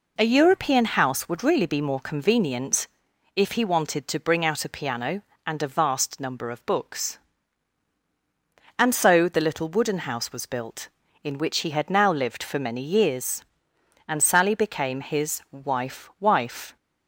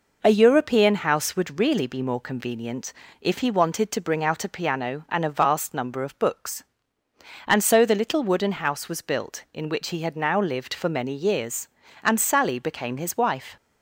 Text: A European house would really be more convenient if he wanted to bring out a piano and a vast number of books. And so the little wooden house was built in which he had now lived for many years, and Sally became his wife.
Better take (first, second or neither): second